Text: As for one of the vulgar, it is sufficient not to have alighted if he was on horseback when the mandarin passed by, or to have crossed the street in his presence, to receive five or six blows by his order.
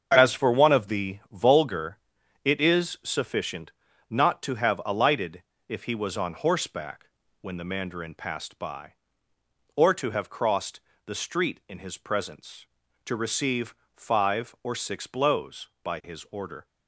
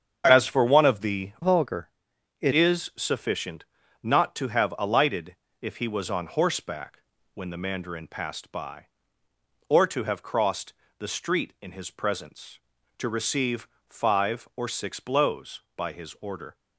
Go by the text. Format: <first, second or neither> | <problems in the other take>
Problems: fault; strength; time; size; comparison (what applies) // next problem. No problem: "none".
first | starts louder than the rest; strong; until 1.3 s; 7.5 dB; also in the first // changes voice from "vulgar" to "it"; from 1.4 to 2.5 s; 1.1 s long // pauses between "sufficient" and "not"; at 3.6 s; 0.38 s long; also in the first // pauses between "alighted" and "if"; slight; at 5.3 s; 0.26 s long; slight in the first // pauses between "horseback" and "when"; slight; at 7.0 s; 0.32 s long; slight in the first // pauses between "crossed" and "the"; slight; at 10.7 s; 0.26 s long; slight in the first // pauses between "receive" and "five"; slight; at 13.6 s; 0.22 s long; slight in the first